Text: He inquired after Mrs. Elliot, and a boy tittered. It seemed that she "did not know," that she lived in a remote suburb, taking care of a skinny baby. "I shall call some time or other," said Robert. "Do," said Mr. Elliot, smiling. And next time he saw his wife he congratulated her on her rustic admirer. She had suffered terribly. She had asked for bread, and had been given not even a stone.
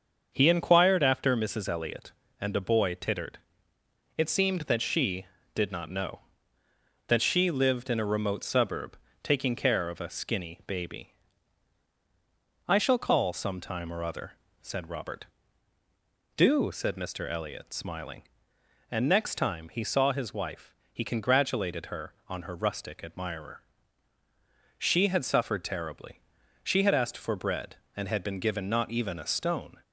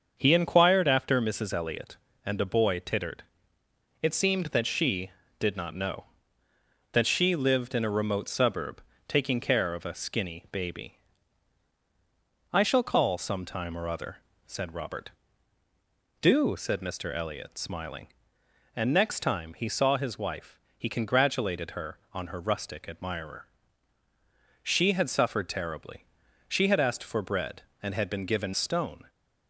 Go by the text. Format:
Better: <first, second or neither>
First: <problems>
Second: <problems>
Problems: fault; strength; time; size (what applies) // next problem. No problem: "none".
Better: first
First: starts louder than the rest; until 1.3 s; 6.5 dB // pauses between "wife" and "he"; slight; at 20.7 s; 0.18 s long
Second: starts louder than the rest; until 1.1 s; 6.5 dB // pauses between "wife" and "he"; slight; at 20.5 s; 0.18 s long // skips "not even a"; at 28.5 s